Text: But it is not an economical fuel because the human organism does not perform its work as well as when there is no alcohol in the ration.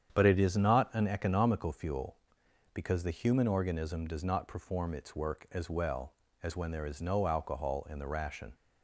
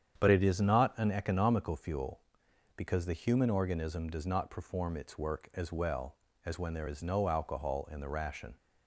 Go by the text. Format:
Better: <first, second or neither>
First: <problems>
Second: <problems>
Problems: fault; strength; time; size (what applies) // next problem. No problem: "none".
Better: neither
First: starts louder than the rest; strong; until 1.1 s; 8.5 dB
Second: starts louder than the rest; strong; until 1.2 s; 8.5 dB